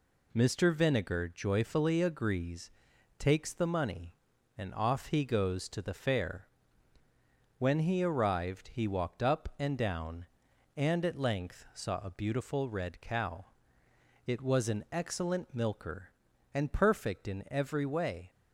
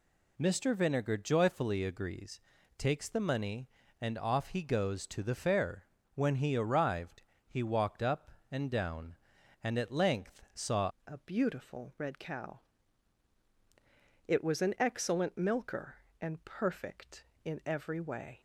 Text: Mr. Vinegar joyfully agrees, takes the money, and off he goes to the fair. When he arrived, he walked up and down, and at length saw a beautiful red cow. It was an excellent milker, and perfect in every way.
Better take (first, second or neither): first